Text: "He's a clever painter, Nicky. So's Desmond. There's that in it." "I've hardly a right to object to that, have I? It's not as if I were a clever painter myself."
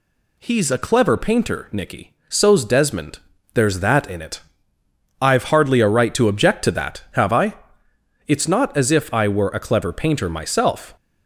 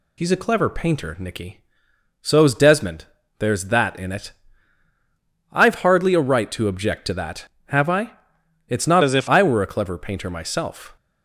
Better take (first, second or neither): first